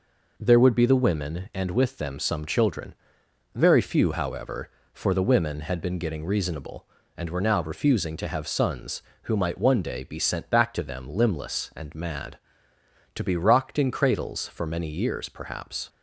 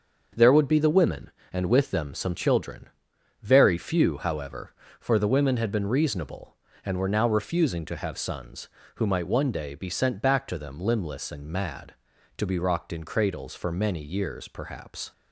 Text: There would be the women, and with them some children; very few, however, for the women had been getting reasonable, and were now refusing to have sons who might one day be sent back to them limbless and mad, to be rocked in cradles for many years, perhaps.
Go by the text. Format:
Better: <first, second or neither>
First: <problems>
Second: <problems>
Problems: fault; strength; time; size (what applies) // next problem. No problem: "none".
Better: first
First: none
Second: starts louder than the rest; until 1.5 s; 6.5 dB // skips "getting"; at 5.8 s